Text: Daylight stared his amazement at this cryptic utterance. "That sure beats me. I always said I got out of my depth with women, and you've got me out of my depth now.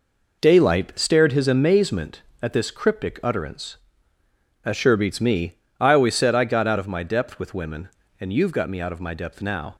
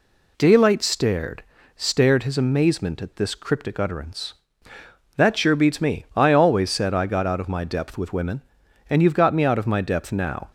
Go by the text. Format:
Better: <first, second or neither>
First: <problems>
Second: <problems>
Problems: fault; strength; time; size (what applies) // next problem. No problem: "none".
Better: first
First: none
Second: says "stared" twice; at 1.7 s